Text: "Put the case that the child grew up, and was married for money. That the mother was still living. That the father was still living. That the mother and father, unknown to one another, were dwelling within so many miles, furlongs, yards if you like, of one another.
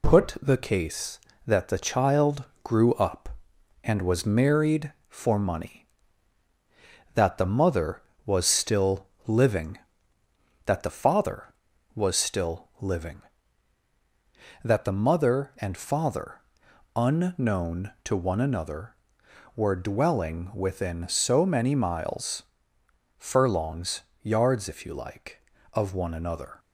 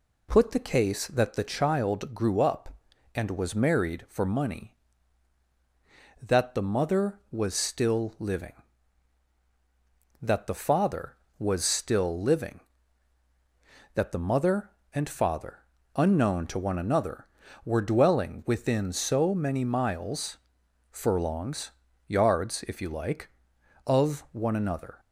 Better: second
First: gets quieter; slight; throughout; 3 dB // pauses between "child" and "grew"; slight; at 2.4 s; 0.18 s long // pauses between "still" and "living"; slight; at 9.0 s; 0.18 s long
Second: none

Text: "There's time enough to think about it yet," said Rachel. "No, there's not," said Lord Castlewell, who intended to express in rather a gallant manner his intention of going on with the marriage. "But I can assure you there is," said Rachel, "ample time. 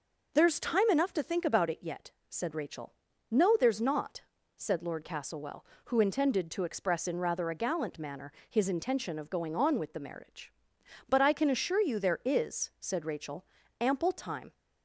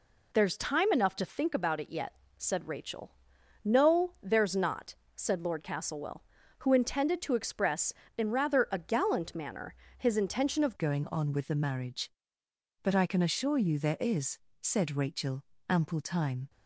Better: first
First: pauses between "manner" and "his"; slight; at 8.3 s; 0.16 s long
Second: pauses between "manner" and "his"; slight; at 9.7 s; 0.24 s long // changes voice at "going"; from 10.7 s on; 5.7 s long

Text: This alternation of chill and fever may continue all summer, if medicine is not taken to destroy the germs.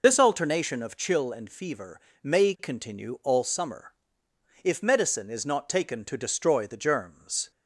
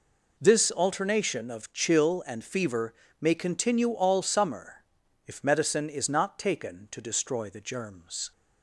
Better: second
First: loses the start of "This"; at 0.0 s; 30 ms // pauses between "fever" and "may"; slight; at 1.9 s; 0.24 s long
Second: pauses between "fever" and "may"; slight; at 2.9 s; 0.28 s long

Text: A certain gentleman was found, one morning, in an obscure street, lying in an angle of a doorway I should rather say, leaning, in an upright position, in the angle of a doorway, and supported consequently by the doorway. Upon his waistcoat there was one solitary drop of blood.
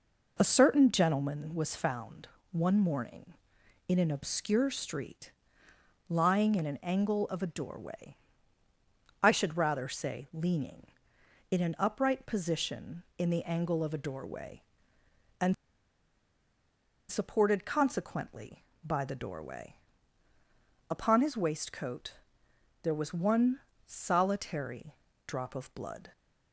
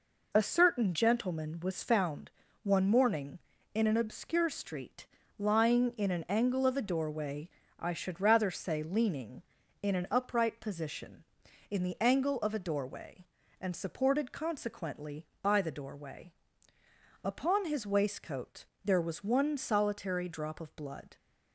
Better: second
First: pauses between "doorway" and "I"; at 8.1 s; 1.0 s long // pauses between "and" and "supported"; strong; at 15.5 s; 1.5 s long // pauses between "waistcoat" and "there"; noticeable; at 22.1 s; 0.70 s long // pauses between "one" and "solitary"; slight; at 23.5 s; 0.28 s long // pauses between "solitary" and "drop"; slight; at 24.9 s; 0.32 s long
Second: pauses between "doorway" and "I"; slight; at 7.4 s; 0.30 s long // pauses between "waistcoat" and "there"; slight; at 18.6 s; 0.18 s long

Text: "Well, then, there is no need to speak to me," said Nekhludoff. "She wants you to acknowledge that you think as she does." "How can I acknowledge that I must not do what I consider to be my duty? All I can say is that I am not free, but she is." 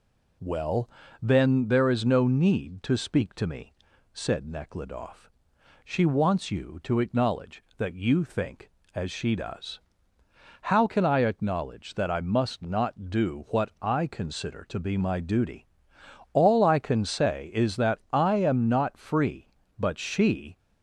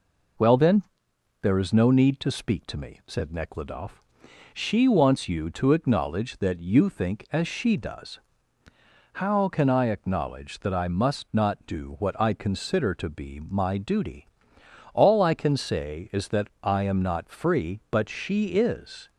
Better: second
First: pauses between "that" and "I"; slight; at 17.9 s; 0.16 s long // stops before "is"; at 20.5 s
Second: none

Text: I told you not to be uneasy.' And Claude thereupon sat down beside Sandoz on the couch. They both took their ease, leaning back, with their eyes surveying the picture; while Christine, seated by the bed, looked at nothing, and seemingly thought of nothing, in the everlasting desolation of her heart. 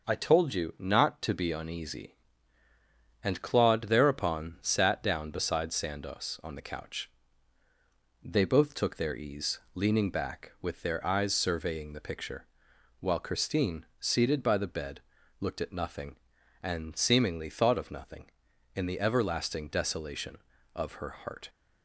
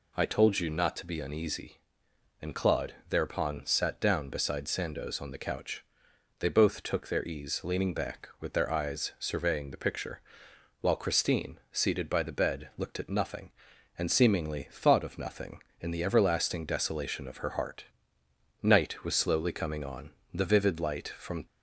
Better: first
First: none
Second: pauses between "Claude" and "thereupon"; slight; at 2.9 s; 0.16 s long // goes on to say "Night was slowly coming on the vivid light from"; strong; from 18.6 s on; 2.8 s long

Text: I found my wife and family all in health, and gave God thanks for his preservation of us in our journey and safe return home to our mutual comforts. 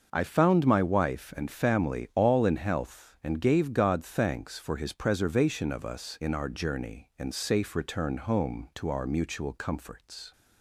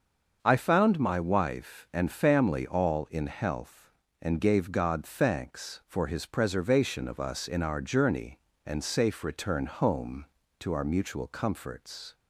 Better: neither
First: starts louder than the rest; noticeable; until 1.1 s; 6 dB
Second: starts louder than the rest; until 1.4 s; 6.5 dB

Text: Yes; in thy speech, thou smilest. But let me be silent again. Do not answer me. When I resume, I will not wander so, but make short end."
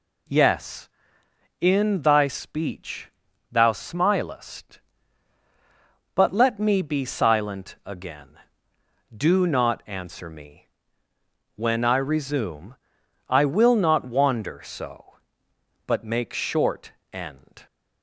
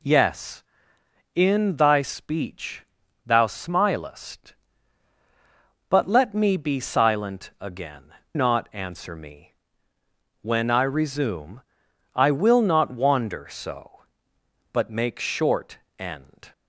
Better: first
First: pauses between "short" and "end"; slight; at 16.9 s; 0.20 s long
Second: skips "Do"; at 8.2 s // pauses between "short" and "end"; slight; at 15.7 s; 0.20 s long

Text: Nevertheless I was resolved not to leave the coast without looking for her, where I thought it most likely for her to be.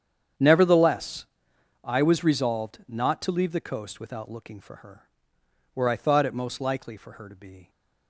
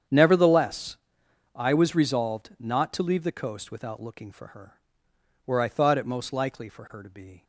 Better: neither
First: starts louder than the rest; strong; until 1.9 s; 8.5 dB // pauses between "Nevertheless" and "I"; noticeable; at 1.2 s; 0.58 s long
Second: starts louder than the rest; strong; until 1.6 s; 8.5 dB // pauses between "Nevertheless" and "I"; noticeable; at 0.9 s; 0.58 s long

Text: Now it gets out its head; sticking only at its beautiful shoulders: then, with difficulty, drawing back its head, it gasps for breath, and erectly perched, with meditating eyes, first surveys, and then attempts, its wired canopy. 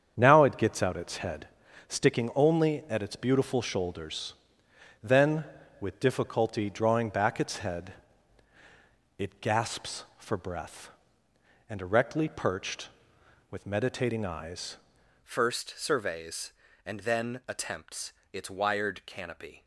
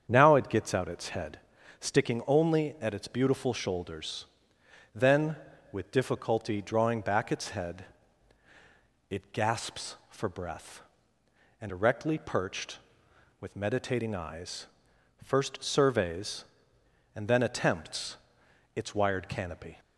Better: second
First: starts louder than the rest; strong; until 1.1 s; 8 dB // changes voice at "first"; from 15.2 s on; 4.4 s long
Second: starts louder than the rest; strong; until 1.1 s; 7.5 dB

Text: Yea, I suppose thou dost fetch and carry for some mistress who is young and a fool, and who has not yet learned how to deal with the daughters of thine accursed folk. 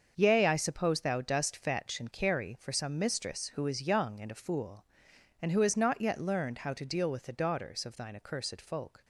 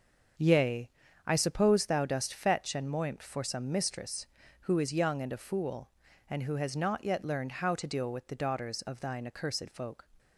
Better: first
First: starts louder than the rest; until 1.1 s; 6.5 dB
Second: starts louder than the rest; until 1.7 s; 7 dB // says "moimt" for "carry"; at 2.8 s

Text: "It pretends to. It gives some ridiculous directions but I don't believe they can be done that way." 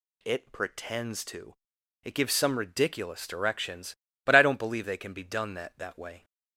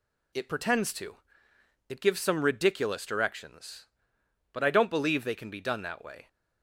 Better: second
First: says "that" twice; at 5.7 s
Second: none

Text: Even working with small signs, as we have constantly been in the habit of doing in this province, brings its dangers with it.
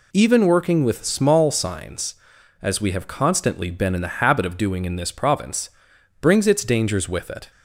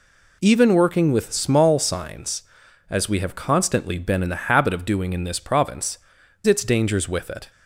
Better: first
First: none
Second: skips "brings"; at 6.2 s

